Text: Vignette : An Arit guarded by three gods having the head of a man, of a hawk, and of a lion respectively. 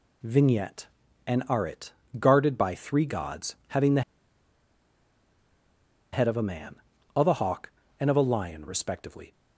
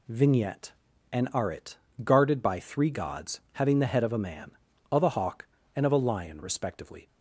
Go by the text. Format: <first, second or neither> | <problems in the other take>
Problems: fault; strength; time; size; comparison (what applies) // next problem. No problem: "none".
second | pauses between "Arit" and "guarded"; slight; at 1.9 s; 0.26 s long; slight in the second // pauses between "the" and "head"; strong; at 4.0 s; 2.1 s long